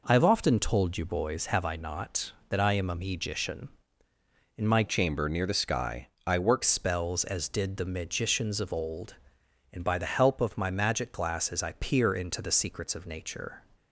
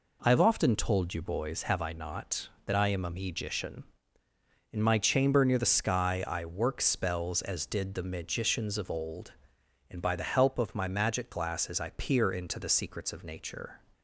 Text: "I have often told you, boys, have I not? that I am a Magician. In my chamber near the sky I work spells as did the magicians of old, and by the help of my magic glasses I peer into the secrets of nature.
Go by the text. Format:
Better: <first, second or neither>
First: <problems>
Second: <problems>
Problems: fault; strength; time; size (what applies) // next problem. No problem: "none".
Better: second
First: changes voice from "chamber" to "work"; from 4.8 to 6.6 s; 1.8 s long // pauses between "sky" and "I"; slight; at 6.0 s; 0.18 s long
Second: none